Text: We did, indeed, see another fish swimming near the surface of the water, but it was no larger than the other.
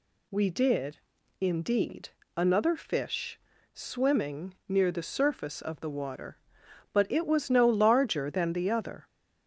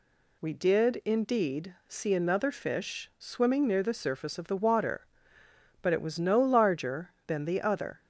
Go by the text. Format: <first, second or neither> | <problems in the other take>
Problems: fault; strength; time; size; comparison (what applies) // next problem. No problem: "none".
second | skips "see"; at 2.2 s // pauses between "fish" and "swimming"; slight; at 3.3 s; 0.34 s long